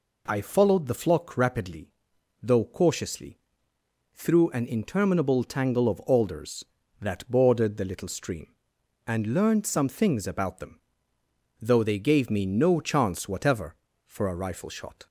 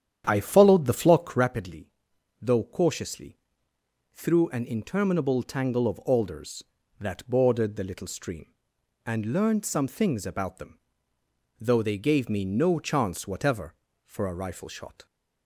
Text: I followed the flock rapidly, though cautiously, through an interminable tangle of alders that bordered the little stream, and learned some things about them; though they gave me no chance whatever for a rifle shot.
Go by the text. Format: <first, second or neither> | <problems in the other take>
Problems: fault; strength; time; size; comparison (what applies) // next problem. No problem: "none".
first | starts louder than the rest; strong; until 1.5 s; 9.5 dB